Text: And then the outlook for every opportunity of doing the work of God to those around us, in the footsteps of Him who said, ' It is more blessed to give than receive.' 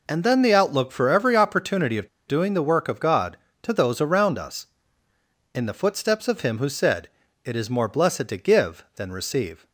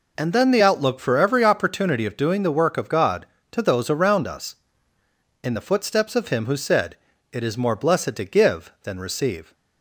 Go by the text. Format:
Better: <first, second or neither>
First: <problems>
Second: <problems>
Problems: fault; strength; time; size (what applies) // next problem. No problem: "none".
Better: second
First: pauses between "of" and "doing"; slight; at 2.0 s; 0.20 s long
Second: none